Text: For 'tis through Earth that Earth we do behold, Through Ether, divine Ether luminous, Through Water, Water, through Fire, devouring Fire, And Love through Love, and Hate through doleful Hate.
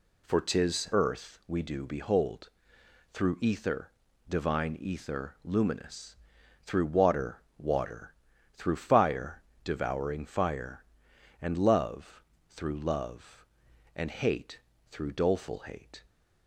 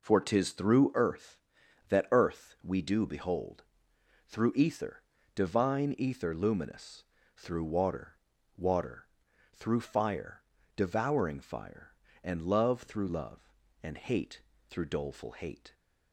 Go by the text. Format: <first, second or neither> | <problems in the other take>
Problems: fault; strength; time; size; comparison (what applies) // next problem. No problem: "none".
second | skips "through Earth that"; at 0.9 s // pauses between "Love" and "through"; slight; at 12.2 s; 0.26 s long // pauses between "Hate" and "through"; slight; at 14.6 s; 0.28 s long; slight in the second